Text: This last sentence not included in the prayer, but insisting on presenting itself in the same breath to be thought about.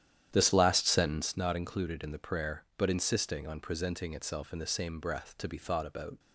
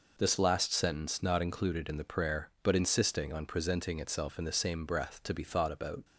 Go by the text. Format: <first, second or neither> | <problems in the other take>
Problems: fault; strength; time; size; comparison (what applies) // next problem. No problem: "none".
second | starts louder than the rest; strong; until 1.4 s; 10.5 dB